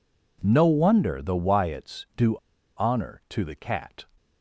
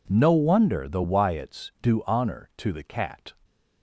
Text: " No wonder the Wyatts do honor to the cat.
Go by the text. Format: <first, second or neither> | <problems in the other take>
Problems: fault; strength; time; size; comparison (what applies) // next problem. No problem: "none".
second | pauses between "do" and "honor"; at 2.3 s; 0.39 s long